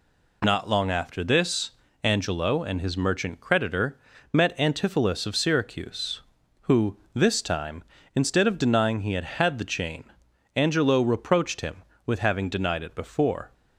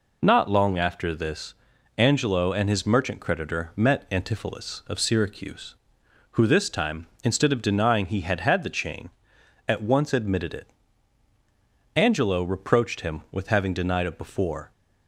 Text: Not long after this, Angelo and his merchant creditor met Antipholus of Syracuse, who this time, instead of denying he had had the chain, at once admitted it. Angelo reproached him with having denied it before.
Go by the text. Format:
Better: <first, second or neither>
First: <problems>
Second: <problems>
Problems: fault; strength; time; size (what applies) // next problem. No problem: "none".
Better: second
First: pauses between "creditor" and "met"; slight; at 3.9 s; 0.36 s long // pauses between "who" and "this"; slight; at 6.9 s; 0.16 s long // skips "at once admitted it"; at 10.2 s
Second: none